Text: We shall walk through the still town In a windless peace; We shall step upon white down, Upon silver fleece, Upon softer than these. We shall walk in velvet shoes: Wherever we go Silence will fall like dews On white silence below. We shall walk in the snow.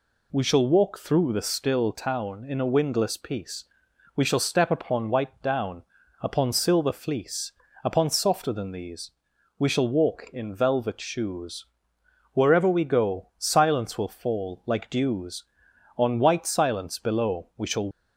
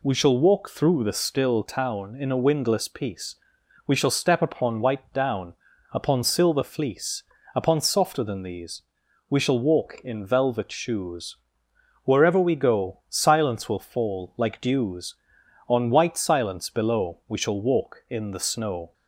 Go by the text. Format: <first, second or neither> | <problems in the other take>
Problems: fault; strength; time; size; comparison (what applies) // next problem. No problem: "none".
second | stops before "walk in the snow"; at 17.9 s